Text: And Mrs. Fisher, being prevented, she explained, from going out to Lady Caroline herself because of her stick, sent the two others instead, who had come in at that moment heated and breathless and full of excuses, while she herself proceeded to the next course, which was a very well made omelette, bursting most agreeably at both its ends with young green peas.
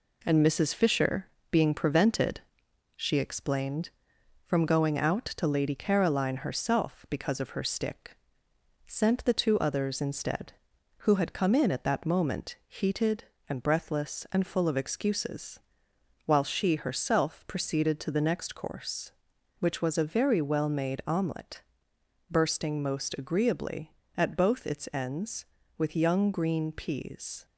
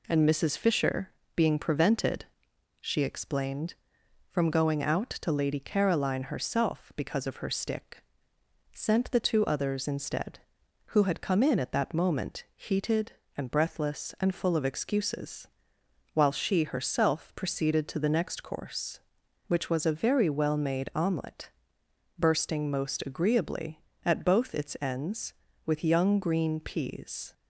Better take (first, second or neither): second